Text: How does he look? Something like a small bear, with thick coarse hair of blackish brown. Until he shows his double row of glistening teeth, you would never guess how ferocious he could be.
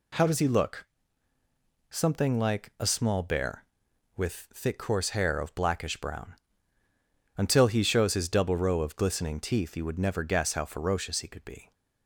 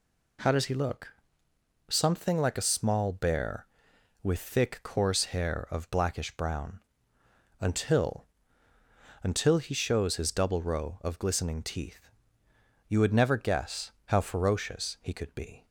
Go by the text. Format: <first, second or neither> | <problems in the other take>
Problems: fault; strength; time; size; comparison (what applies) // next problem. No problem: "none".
first | says "Until" twice; at 9.2 s